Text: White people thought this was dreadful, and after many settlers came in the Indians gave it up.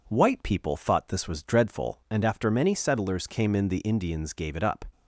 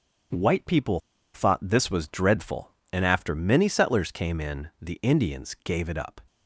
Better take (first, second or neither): first